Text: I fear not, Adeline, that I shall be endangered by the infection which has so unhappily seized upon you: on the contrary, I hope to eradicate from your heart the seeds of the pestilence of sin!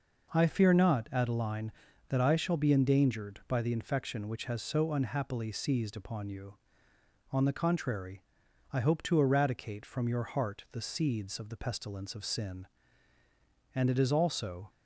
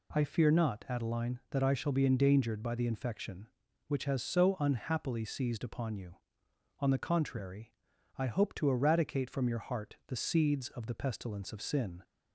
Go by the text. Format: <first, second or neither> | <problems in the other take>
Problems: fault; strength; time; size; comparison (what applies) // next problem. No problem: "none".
second | goes on to say "And it is also"; noticeable; from 13.7 s on; 0.96 s long